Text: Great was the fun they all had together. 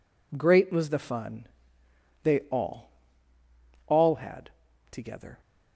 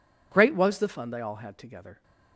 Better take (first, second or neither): second